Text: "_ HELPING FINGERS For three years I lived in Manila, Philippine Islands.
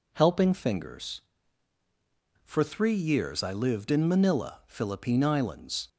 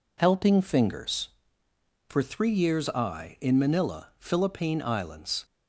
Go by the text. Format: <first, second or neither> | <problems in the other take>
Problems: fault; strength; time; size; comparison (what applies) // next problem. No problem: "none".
first | skips "lived"; at 3.3 s